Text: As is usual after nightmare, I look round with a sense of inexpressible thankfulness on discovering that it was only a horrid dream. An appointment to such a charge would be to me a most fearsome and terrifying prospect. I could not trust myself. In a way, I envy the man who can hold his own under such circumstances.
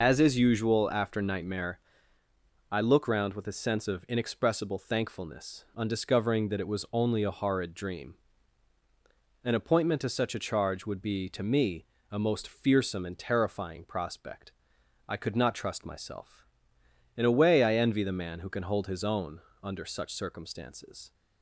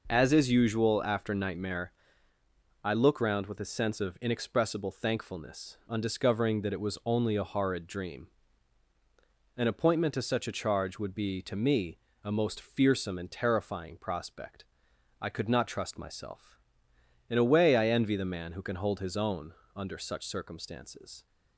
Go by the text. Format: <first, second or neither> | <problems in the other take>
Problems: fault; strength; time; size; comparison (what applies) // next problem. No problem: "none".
second | loses the start of "As"; at 0.0 s; 85 ms // pauses between "me" and "a"; slight; at 11.8 s; 0.26 s long; slight in the second // pauses between "own" and "under"; slight; at 19.4 s; 0.20 s long; slight in the second